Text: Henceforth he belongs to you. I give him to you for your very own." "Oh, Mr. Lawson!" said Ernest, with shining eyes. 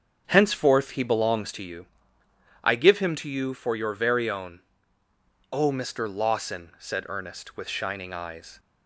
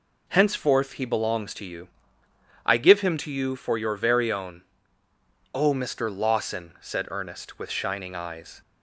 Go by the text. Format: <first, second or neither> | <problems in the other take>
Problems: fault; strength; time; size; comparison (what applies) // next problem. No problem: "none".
second | starts louder than the rest; strong; until 1.7 s; 7.5 dB